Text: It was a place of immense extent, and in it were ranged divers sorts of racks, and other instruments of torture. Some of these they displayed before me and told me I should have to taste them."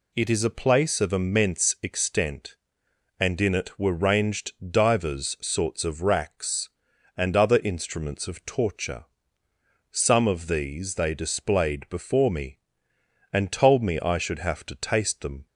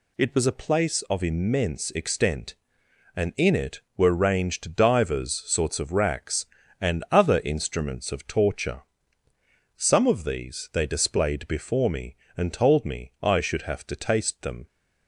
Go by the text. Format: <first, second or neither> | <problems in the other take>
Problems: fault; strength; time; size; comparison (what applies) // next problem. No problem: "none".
second | says "is" for "was"; at 0.2 s // pauses between "ranged" and "divers"; slight; at 4.5 s; 0.18 s long